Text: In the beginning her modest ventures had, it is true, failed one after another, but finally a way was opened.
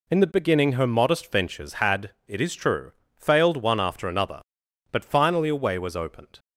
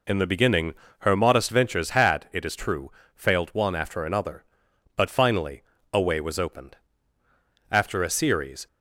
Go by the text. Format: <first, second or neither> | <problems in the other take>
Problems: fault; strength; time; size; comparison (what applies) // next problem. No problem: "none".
first | pauses between "beginning" and "her"; slight; at 0.7 s; 0.24 s long // pauses between "finally" and "a"; slight; at 5.6 s; 0.30 s long // goes on to say "After a series"; noticeable; from 7.7 s on; 0.96 s long